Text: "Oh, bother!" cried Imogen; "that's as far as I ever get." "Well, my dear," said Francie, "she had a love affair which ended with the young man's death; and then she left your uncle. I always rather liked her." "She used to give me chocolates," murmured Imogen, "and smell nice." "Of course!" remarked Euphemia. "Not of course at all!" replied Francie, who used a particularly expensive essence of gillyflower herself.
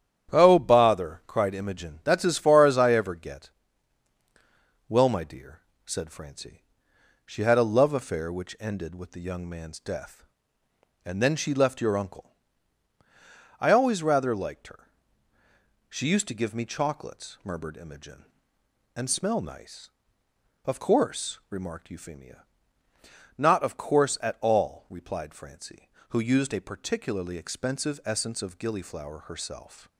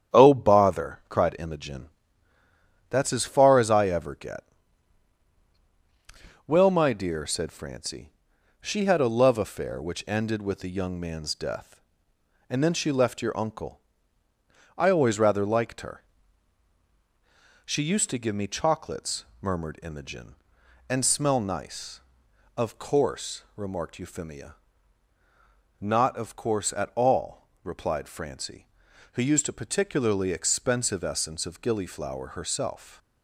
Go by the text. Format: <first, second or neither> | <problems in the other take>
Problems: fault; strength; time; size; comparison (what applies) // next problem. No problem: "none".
neither | starts louder than the rest; strong; the same in both